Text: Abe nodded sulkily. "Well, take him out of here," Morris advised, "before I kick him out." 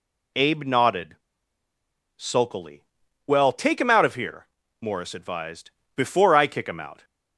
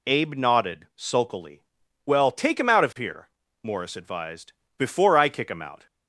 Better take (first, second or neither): second